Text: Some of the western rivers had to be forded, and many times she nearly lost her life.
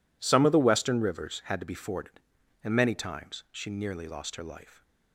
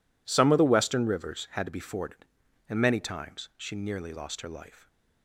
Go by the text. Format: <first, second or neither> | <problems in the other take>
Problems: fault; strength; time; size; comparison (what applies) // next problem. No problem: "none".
neither | none